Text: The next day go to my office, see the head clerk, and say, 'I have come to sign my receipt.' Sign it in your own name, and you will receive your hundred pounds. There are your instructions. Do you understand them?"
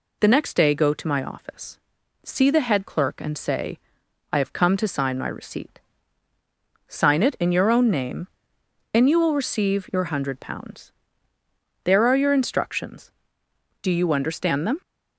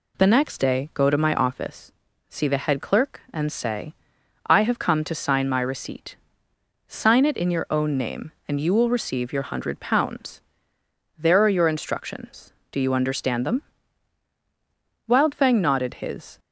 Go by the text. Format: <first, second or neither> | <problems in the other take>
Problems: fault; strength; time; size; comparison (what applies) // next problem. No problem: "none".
first | goes on to say "Wildfang nodded his"; from 15.0 s on; 1.3 s long